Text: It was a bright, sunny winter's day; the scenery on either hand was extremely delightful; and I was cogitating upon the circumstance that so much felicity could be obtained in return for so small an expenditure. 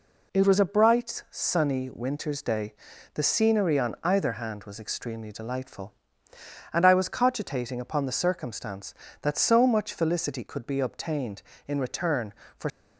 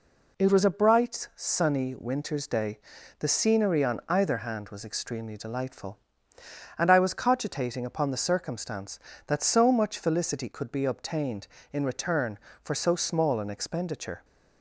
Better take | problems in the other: second | stops before "so small an expenditure"; at 12.6 s

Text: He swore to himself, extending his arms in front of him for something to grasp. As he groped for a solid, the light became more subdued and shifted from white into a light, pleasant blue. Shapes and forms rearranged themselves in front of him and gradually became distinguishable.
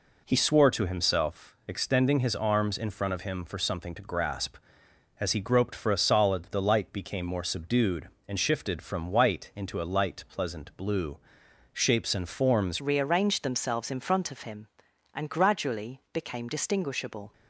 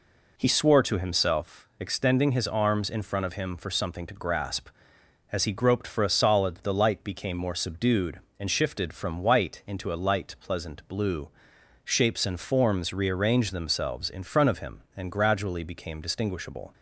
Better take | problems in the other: second | changes voice at "rearranged"; from 12.7 s on; 4.6 s long

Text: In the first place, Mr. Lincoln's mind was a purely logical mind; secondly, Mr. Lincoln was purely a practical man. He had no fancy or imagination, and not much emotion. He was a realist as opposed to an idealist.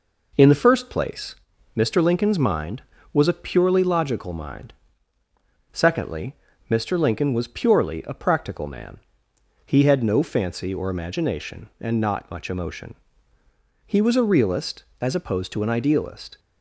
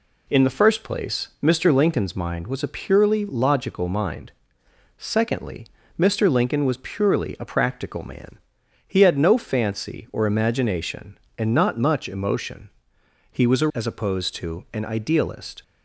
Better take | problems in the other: first | skips "realist"; at 13.7 s

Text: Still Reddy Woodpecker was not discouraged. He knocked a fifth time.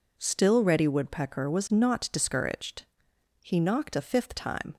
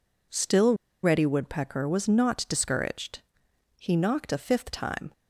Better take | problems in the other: first | pauses between "Still" and "Reddy"; slight; at 0.7 s; 0.28 s long

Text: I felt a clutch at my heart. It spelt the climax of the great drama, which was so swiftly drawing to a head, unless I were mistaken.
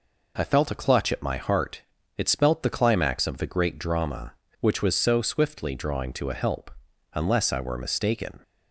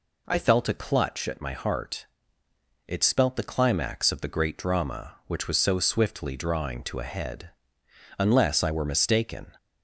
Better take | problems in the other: second | says "help" for "head"; at 6.3 s

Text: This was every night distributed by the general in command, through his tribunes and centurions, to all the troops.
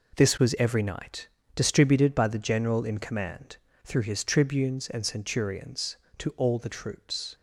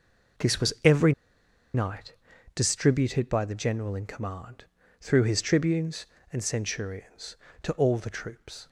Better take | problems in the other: first | pauses between "every" and "night"; noticeable; at 1.1 s; 0.62 s long // pauses between "night" and "distributed"; at 2.1 s; 0.40 s long; slight in the first

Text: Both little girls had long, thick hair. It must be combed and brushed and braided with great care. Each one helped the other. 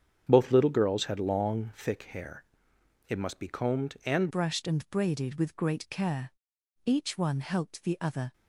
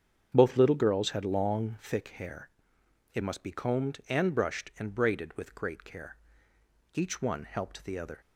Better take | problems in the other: second | starts louder than the rest; strong; until 1.2 s; 8 dB; strong in the second // changes voice at "brushed"; from 4.3 s on; 4.0 s long

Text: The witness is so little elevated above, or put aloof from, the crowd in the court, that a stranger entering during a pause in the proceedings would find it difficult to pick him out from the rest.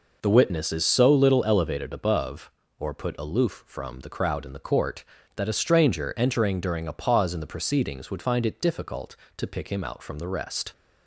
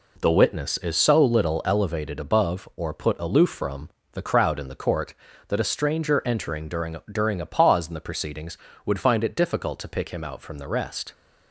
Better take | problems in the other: first | says "during" twice; at 7.1 s

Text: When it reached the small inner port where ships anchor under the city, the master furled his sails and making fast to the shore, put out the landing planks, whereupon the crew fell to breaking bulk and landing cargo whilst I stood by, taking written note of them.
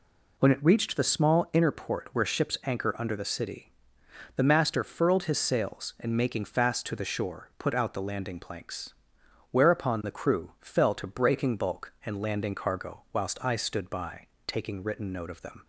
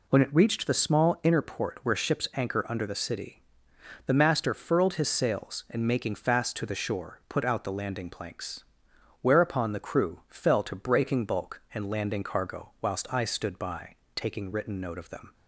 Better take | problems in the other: neither | none

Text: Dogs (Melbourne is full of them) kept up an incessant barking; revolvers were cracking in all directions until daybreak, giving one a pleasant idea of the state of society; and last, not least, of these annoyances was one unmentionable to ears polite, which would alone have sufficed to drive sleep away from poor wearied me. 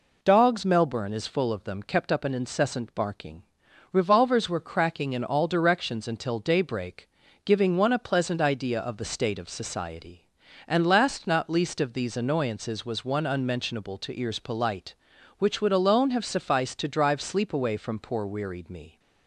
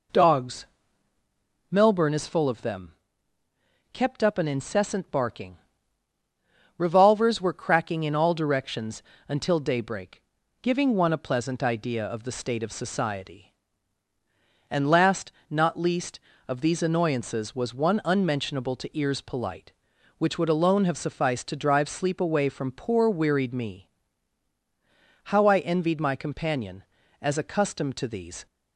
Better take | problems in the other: first | pauses between "directions" and "until"; slight; at 9.0 s; 0.24 s long // goes on to say "How I envied my companion as accustomed to these"; strong; from 25.2 s on; 3.2 s long

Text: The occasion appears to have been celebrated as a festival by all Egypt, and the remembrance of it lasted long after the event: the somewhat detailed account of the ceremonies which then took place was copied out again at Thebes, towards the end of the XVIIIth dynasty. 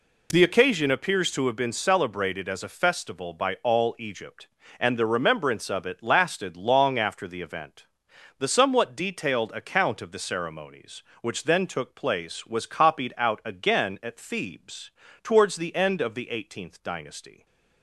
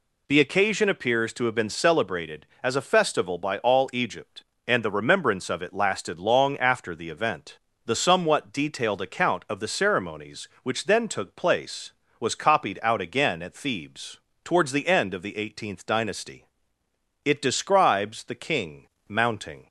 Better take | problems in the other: first | goes on to say "It describes the king mounting"; strong; from 17.2 s on; 2.4 s long

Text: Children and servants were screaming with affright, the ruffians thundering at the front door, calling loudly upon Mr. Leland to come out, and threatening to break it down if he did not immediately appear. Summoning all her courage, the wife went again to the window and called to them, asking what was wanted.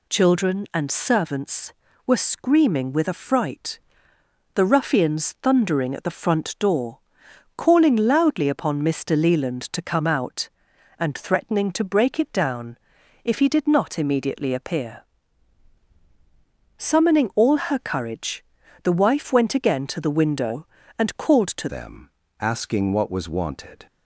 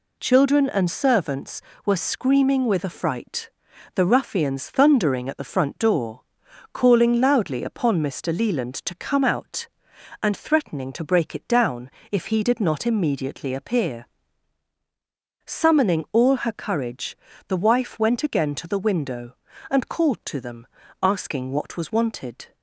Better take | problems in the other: second | pauses between "down" and "if"; noticeable; at 12.7 s; 0.46 s long; slight in the second // changes voice at "them"; from 21.6 s on; 2.2 s long

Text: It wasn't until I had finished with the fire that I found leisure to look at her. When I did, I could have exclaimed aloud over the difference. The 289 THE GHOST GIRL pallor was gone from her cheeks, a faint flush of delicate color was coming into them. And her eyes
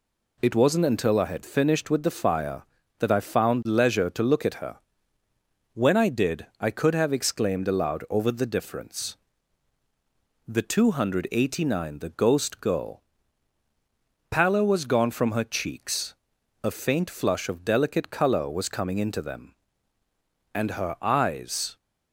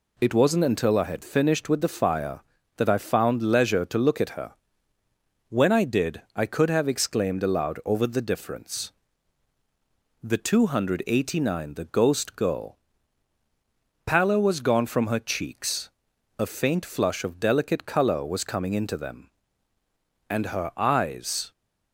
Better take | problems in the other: neither | pauses between "GIRL" and "pallor"; strong; the same in both

